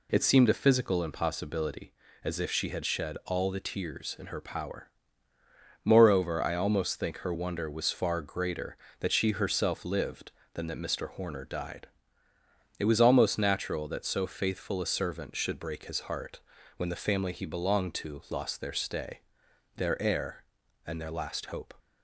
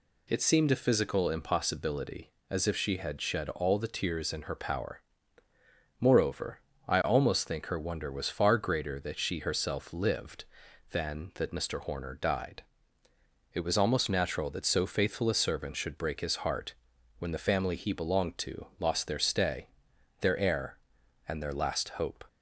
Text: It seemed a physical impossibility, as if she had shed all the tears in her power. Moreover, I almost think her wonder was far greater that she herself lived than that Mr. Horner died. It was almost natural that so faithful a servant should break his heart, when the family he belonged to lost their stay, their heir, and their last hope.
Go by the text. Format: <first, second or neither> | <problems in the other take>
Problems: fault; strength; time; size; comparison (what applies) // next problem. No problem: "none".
neither | none